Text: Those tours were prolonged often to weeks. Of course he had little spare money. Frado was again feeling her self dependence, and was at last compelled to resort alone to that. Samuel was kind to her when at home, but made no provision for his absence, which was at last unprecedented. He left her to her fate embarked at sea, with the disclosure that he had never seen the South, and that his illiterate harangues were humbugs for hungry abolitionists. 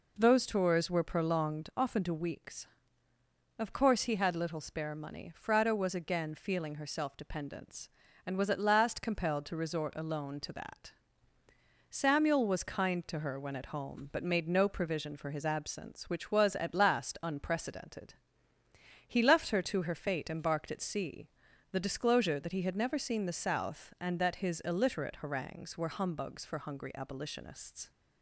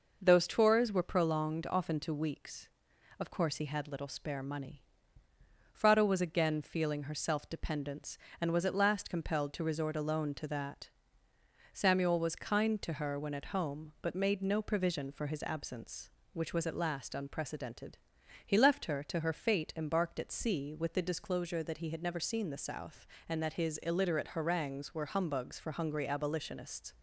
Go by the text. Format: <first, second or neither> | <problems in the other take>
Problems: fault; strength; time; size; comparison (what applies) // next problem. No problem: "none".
second | skips "with"; at 21.5 s